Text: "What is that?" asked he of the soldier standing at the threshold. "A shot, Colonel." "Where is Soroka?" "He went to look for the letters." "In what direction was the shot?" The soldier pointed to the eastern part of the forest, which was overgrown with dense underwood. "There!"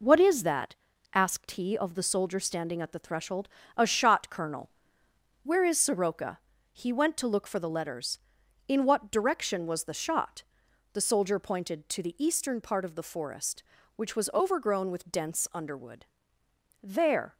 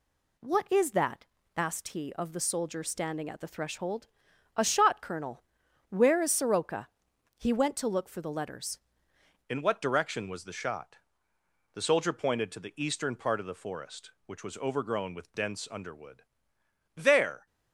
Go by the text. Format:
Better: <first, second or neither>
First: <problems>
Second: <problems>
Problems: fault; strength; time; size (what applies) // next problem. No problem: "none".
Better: first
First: none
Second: changes voice at "In"; from 9.4 s on; 8.0 s long